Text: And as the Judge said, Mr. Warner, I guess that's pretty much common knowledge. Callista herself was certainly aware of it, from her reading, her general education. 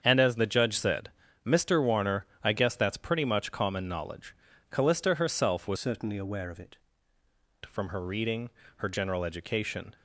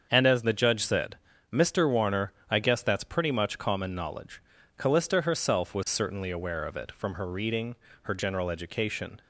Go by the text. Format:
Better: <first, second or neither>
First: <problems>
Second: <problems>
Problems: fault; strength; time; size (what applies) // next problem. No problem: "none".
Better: second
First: starts louder than the rest; strong; until 1.0 s; 7 dB // changes voice from "certainly" to "it"; from 5.7 to 6.7 s; 1.0 s long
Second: starts louder than the rest; until 1.1 s; 7 dB